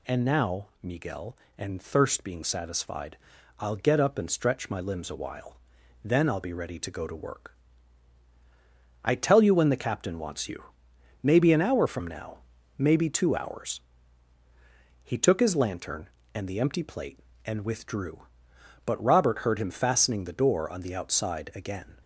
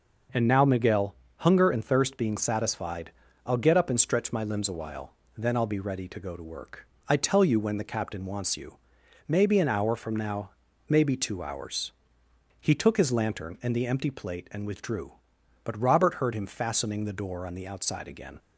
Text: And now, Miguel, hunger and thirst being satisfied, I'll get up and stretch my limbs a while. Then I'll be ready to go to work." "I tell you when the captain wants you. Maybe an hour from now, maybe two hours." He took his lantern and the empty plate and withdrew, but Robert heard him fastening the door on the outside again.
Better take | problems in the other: second | skips "hunger"; at 1.4 s

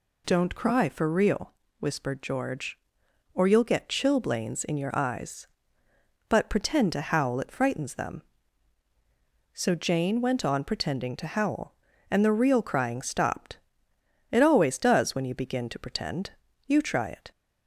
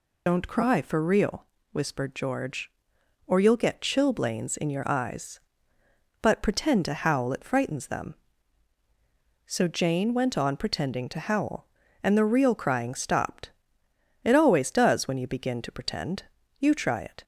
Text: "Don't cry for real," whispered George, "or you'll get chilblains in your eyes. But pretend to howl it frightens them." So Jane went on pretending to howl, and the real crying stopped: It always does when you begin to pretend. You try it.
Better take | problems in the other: first | loses the start of "Don't"; at 0.2 s; 80 ms

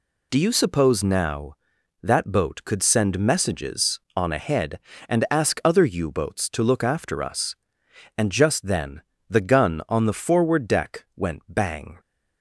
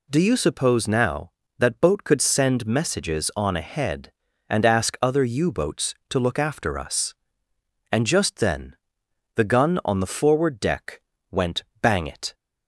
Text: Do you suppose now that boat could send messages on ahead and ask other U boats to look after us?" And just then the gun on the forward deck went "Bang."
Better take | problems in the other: first | pauses between "then" and "the"; noticeable; at 8.7 s; 0.58 s long; slight in the first // pauses between "deck" and "went"; slight; at 11.0 s; 0.28 s long // pauses between "went" and "Bang"; slight; at 11.6 s; 0.20 s long // goes on to say "It"; slight; from 12.0 s on; 0.28 s long

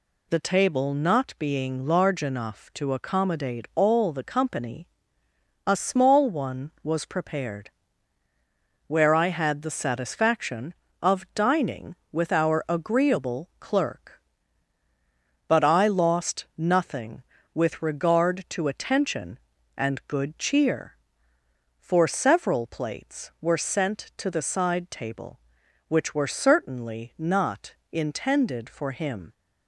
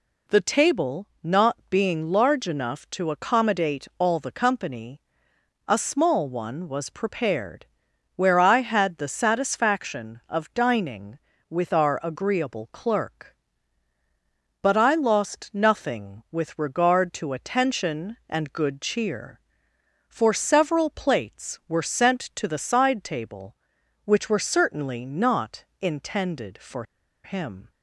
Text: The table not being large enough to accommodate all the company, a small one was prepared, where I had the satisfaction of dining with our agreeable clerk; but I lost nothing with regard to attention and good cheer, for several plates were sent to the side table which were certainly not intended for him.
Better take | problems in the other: first | pauses between "table" and "not"; slight; at 1.0 s; 0.16 s long // pauses between "not" and "intended"; slight; at 25.6 s; 0.16 s long; slight in the first // pauses between "for" and "him"; at 26.8 s; 0.41 s long

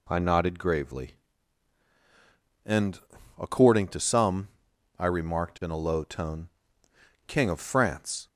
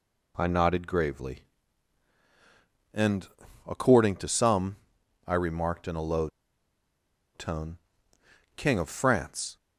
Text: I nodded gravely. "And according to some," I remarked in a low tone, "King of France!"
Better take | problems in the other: first | pauses between "And" and "according"; at 3.2 s; 0.38 s long; also in the first // pauses between "low" and "tone"; at 6.2 s; 1.0 s long

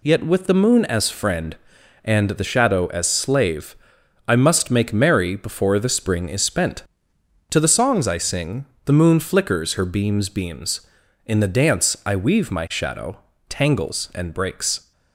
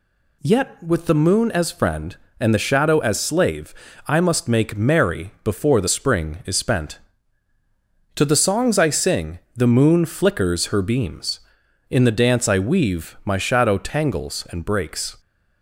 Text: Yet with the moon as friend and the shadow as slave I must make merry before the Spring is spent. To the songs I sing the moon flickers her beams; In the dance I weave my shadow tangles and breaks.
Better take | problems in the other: second | pauses between "slave" and "I"; noticeable; at 3.7 s; 0.52 s long; slight in the second // pauses between "sing" and "the"; slight; at 8.6 s; 0.20 s long; slight in the second // says "beams" twice; at 10.2 s // pauses between "shadow" and "tangles"; slight; at 13.1 s; 0.32 s long

